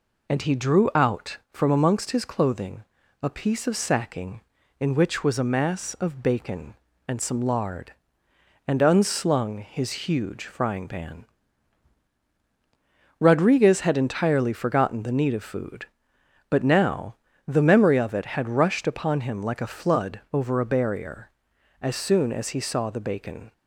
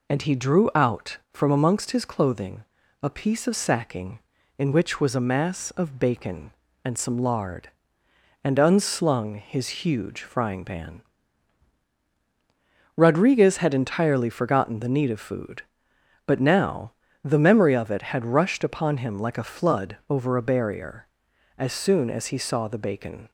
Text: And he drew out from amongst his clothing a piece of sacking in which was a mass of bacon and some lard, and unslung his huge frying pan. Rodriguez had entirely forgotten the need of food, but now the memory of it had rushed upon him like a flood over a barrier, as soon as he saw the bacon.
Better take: neither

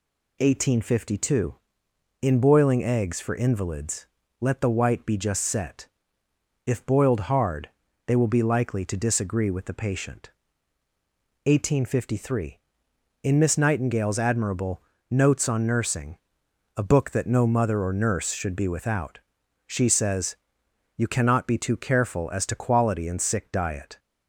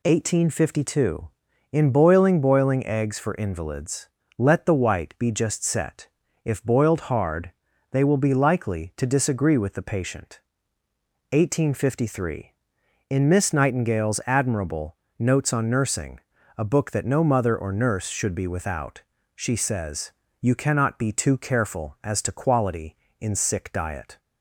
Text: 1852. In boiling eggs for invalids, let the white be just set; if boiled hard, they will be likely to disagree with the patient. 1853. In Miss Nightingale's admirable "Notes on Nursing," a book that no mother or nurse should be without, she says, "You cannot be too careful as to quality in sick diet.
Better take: first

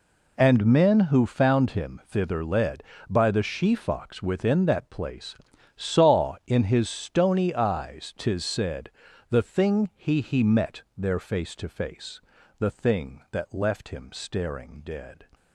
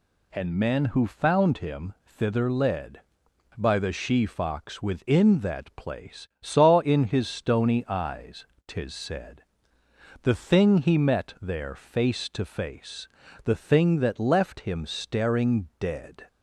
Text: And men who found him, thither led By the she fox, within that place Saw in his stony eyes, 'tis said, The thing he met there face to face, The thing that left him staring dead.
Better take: second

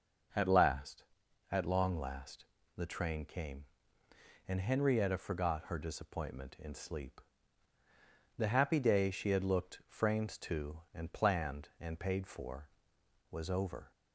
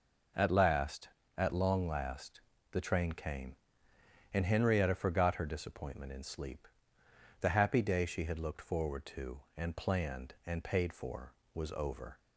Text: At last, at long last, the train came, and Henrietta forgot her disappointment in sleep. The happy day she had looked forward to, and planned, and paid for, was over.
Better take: second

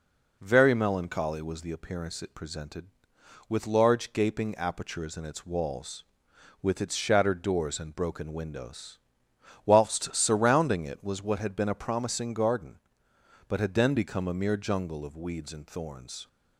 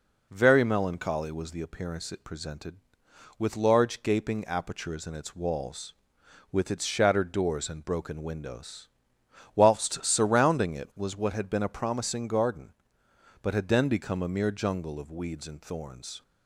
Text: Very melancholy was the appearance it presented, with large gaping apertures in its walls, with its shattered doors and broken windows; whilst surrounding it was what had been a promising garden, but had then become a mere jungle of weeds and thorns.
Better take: neither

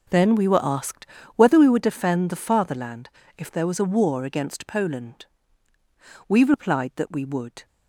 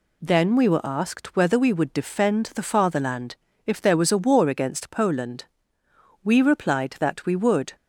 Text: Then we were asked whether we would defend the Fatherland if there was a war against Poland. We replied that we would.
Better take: second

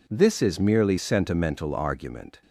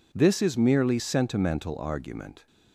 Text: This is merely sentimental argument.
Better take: neither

